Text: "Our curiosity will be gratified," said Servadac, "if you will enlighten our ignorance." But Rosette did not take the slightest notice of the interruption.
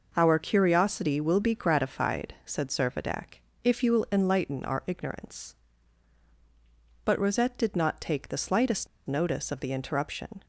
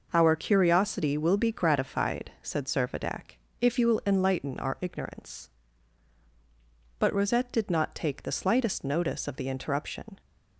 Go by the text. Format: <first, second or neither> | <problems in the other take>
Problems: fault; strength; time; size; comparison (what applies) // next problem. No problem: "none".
second | pauses between "slightest" and "notice"; slight; at 8.8 s; 0.20 s long